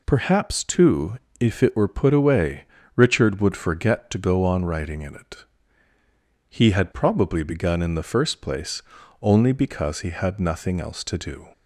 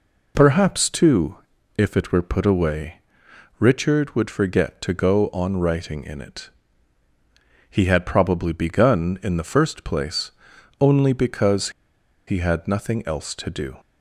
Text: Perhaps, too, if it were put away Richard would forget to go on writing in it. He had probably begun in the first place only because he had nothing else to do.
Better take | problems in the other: first | pauses between "away" and "Richard"; noticeable; at 2.9 s; 0.58 s long; slight in the first // pauses between "place" and "only"; noticeable; at 10.3 s; 0.46 s long; also in the first // pauses between "because" and "he"; noticeable; at 11.6 s; 0.57 s long

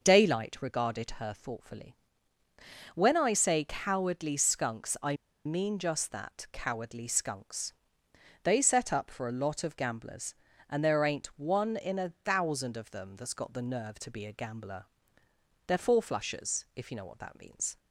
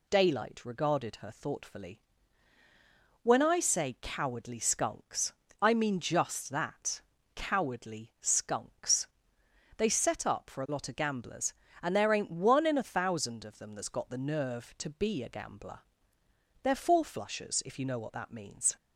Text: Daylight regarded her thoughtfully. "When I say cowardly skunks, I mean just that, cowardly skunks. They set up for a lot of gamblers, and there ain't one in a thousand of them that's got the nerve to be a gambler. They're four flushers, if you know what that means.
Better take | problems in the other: second | pauses between "I" and "mean"; slight; at 5.1 s; 0.30 s long

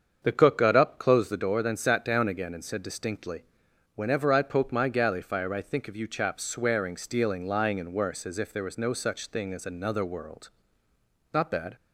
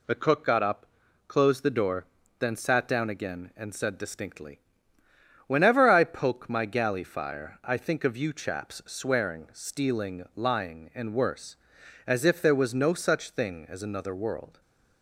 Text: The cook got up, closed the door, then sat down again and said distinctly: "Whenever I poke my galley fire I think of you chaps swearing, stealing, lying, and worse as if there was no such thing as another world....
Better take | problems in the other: second | starts louder than the rest; strong; until 1.2 s; 7 dB // goes on to say "Not bad"; slight; from 11.3 s on; 0.42 s long

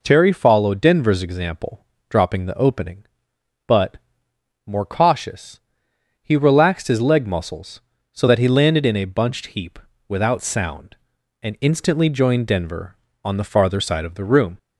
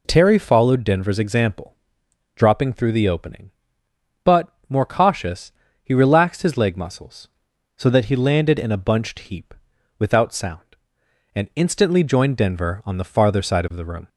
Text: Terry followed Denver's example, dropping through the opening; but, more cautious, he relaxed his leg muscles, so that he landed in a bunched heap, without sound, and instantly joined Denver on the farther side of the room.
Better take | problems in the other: second | skips "through"; at 2.4 s

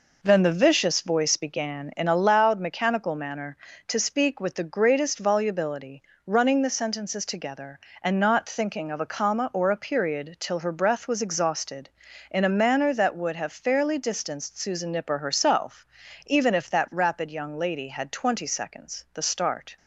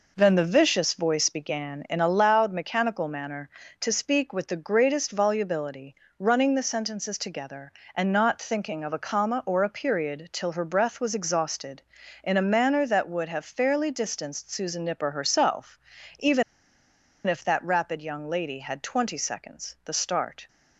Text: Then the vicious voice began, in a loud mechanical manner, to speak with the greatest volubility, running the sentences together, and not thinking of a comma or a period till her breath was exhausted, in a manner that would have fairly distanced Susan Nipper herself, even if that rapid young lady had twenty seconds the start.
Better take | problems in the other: first | pauses between "even" and "if"; noticeable; at 16.4 s; 0.84 s long

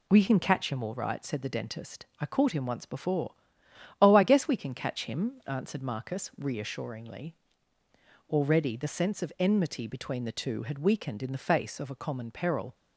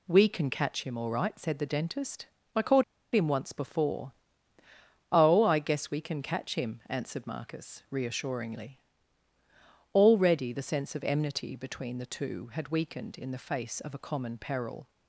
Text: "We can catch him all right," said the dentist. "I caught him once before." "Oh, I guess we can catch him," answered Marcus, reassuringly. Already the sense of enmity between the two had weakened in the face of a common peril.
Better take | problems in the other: first | pauses between "caught" and "him"; slight; at 2.8 s; 0.31 s long

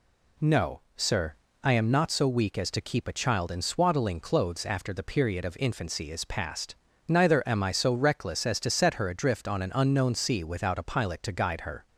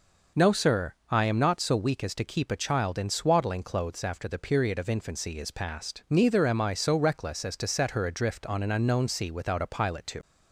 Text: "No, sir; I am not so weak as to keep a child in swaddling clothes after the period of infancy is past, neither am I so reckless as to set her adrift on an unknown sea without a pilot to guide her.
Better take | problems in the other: first | stops before "guide her"; at 10.2 s

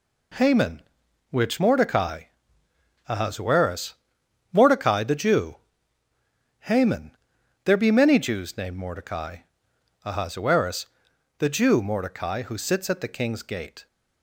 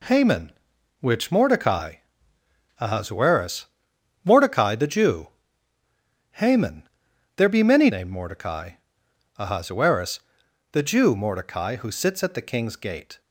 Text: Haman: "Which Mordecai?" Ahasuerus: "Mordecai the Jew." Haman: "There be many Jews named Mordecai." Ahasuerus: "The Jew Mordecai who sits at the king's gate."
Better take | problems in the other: first | skips "Jews"; at 7.8 s

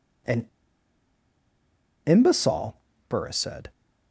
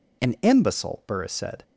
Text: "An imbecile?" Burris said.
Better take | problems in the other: second | pauses between "An" and "imbecile"; strong; at 0.4 s; 1.5 s long

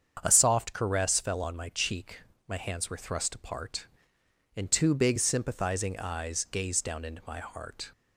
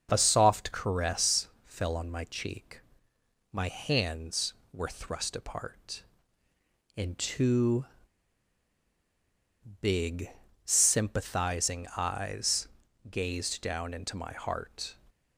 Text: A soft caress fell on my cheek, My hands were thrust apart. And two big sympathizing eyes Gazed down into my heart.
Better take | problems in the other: first | starts louder than the rest; until 1.1 s; 6.5 dB; strong in the first // pauses between "caress" and "fell"; slight; at 1.4 s; 0.18 s long // pauses between "two" and "big"; strong; at 7.8 s; 1.9 s long // pauses between "big" and "sympathizing"; at 10.2 s; 0.38 s long // pauses between "eyes" and "Gazed"; at 12.6 s; 0.42 s long

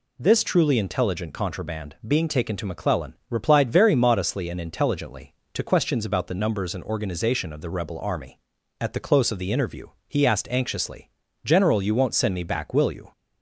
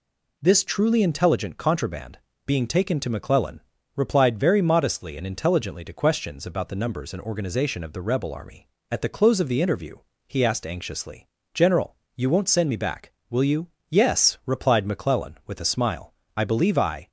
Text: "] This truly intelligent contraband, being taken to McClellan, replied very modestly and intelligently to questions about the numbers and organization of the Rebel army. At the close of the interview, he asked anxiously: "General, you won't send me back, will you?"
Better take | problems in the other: first | goes on to say "Yes replied McClellan with a smile I believe I"; strong; from 13.8 s on; 3.2 s long

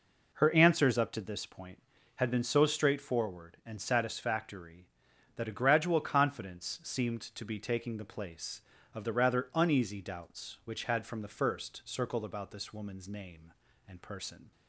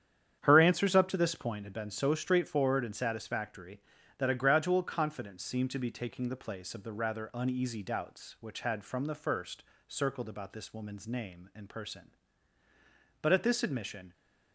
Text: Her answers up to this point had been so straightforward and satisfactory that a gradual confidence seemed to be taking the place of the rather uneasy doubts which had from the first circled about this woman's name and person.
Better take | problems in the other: first | starts louder than the rest; strong; until 1.4 s; 9 dB // pauses between "first" and "circled"; slight; at 9.6 s; 0.24 s long // goes on to say "But at this admission"; noticeable; from 13.2 s on; 0.92 s long

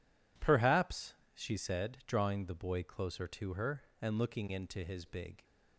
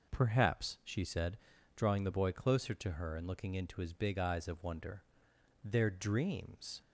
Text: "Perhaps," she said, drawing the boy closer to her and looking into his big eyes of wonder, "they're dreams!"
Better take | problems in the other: second | stops before "eyes of wonder they're dreams"; at 5.4 s

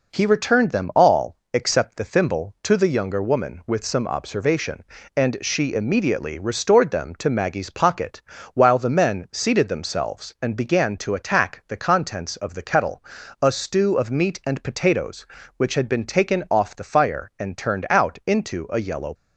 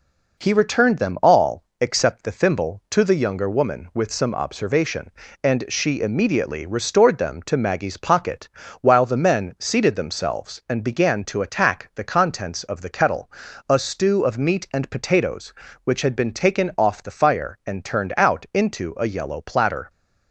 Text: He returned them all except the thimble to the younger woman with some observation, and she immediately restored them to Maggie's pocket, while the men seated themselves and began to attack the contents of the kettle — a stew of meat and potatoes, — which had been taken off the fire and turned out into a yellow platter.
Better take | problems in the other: second | pauses between "all" and "except"; slight; at 1.3 s; 0.18 s long; slight in the second // stops before "platter"; at 19.1 s

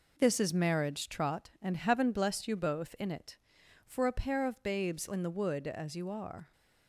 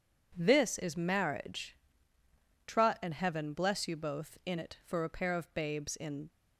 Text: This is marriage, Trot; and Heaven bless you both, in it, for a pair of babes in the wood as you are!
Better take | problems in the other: first | stops before "the wood as you are"; at 6.2 s

